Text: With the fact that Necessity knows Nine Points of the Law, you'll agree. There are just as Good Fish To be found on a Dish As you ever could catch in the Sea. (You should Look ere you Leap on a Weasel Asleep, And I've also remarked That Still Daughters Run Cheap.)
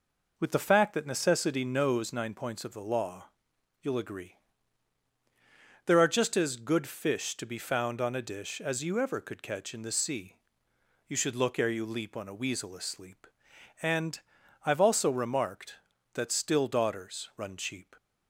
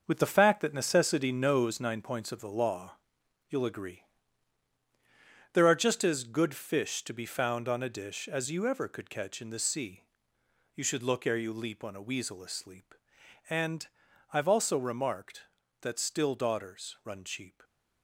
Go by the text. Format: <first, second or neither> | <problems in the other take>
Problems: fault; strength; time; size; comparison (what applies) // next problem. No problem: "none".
first | gets quieter; strong; throughout; 8 dB // pauses between "And" and "I've"; noticeable; at 13.8 s; 0.48 s long; noticeable in the first